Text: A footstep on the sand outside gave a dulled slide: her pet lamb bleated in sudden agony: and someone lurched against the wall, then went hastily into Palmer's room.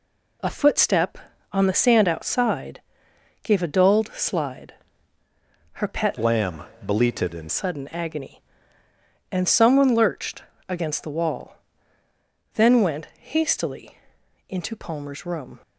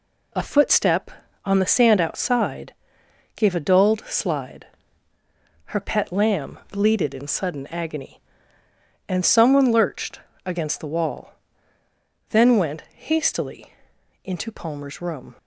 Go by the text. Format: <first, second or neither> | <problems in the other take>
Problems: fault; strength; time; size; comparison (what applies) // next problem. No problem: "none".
second | pauses between "outside" and "gave"; noticeable; at 2.7 s; 0.64 s long; noticeable in the second // changes voice from "lamb" to "in"; from 6.1 to 7.5 s; 1.4 s long // pauses between "lamb" and "bleated"; slight; at 6.6 s; 0.20 s long // pauses between "lurched" and "against"; slight; at 10.4 s; 0.26 s long; slight in the second // pauses between "hastily" and "into"; noticeable; at 13.9 s; 0.50 s long; noticeable in the second